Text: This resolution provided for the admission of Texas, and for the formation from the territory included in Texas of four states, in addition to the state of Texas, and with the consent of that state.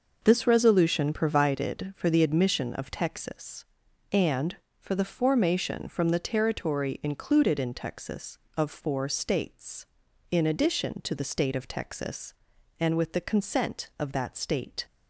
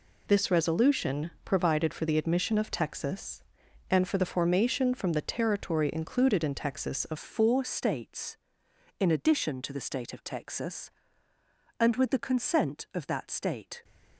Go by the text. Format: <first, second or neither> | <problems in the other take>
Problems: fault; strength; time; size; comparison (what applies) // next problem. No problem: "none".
first | changes voice at "four"; from 7.1 s on; 6.7 s long